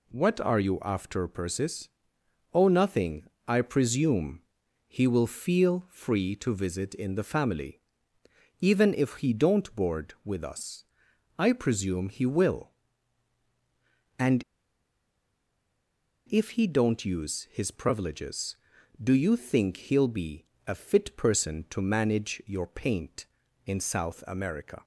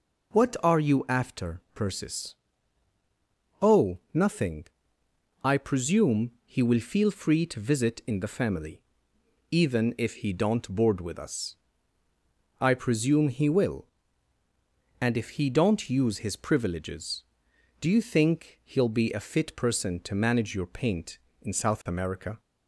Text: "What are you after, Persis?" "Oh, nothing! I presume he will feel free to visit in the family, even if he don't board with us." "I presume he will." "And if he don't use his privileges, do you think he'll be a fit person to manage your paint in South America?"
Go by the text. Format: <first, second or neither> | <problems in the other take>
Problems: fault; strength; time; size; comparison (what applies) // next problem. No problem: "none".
second | pauses between "presume" and "he"; noticeable; at 4.4 s; 0.46 s long // pauses between "And" and "if"; strong; at 14.4 s; 1.8 s long // pauses between "be" and "a"; slight; at 20.4 s; 0.22 s long